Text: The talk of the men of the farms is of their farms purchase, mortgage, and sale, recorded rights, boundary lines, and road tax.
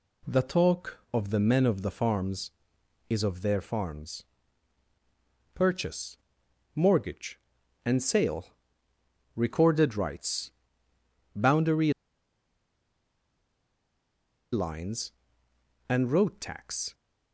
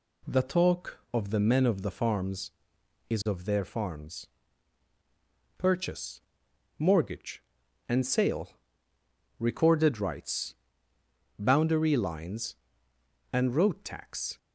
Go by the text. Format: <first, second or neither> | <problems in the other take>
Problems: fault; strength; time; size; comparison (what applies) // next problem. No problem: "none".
second | pauses between "farms" and "purchase"; strong; at 4.2 s; 1.3 s long; strong in the second // pauses between "boundary" and "lines"; strong; at 11.9 s; 2.6 s long